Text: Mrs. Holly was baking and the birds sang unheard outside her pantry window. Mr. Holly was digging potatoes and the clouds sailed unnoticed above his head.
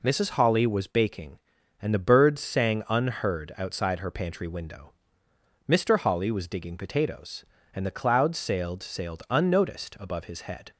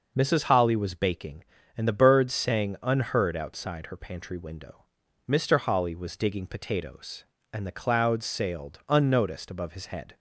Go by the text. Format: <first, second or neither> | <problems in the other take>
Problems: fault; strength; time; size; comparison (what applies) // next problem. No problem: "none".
second | says "sailed" twice; at 8.8 s